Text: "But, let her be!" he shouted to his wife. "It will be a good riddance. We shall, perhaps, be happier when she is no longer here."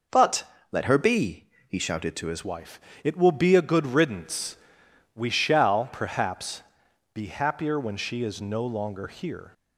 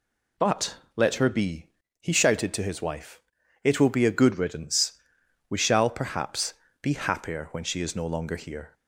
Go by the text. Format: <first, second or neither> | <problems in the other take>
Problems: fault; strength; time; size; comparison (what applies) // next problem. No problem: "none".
second | changes voice at "wife"; from 2.4 s on; 7.1 s long